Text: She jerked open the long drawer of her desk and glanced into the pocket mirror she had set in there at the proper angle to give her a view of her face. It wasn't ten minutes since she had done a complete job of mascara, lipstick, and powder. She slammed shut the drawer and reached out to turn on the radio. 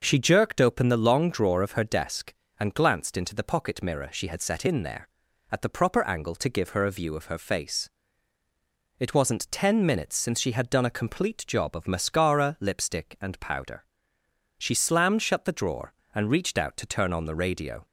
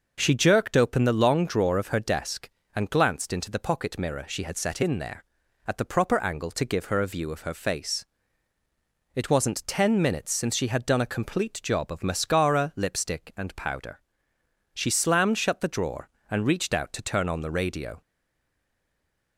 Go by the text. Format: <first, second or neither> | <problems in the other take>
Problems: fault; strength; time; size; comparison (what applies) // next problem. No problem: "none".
first | stays silent after the last word; noticeable; from 18.0 s on; 1.3 s long